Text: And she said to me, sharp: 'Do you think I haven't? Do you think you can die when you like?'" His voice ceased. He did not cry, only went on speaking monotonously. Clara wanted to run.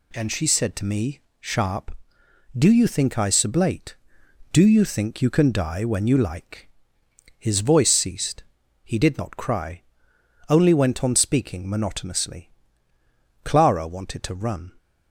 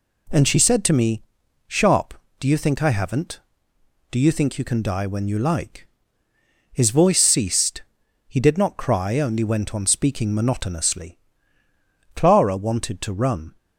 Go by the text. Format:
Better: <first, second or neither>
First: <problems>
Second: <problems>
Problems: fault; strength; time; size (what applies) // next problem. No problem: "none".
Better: second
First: says "sublate" for "haven't"; at 3.2 s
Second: none